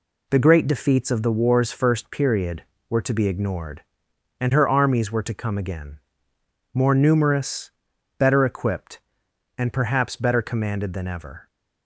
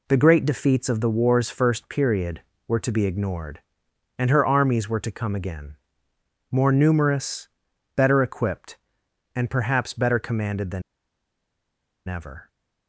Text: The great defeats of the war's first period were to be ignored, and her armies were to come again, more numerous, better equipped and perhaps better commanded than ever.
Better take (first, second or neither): first